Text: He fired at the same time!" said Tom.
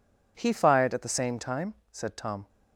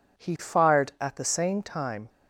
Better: first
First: none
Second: stops before "said Tom"; at 2.0 s

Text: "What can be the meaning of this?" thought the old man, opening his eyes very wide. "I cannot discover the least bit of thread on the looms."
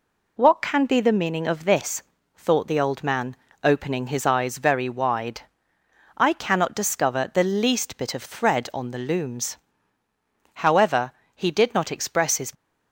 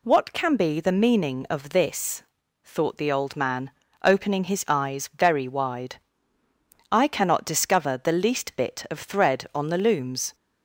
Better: second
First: goes on to say "However he did not express his"; strong; from 10.6 s on; 1.9 s long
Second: none

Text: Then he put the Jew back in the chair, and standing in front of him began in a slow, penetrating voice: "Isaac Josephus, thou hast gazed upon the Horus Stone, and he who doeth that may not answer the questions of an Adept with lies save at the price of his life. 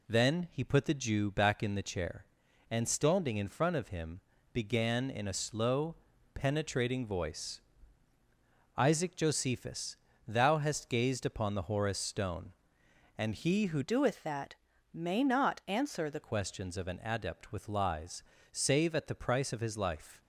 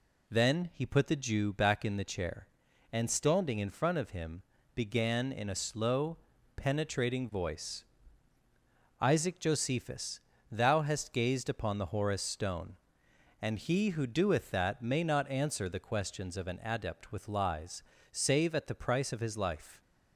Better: second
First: pauses between "him" and "began"; slight; at 4.1 s; 0.32 s long // changes voice from "doeth" to "the"; from 13.8 to 16.2 s; 2.4 s long // pauses between "that" and "may"; at 14.5 s; 0.38 s long // pauses between "lies" and "save"; slight; at 18.2 s; 0.28 s long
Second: pauses between "him" and "began"; slight; at 4.4 s; 0.32 s long // pauses between "lies" and "save"; slight; at 17.8 s; 0.28 s long

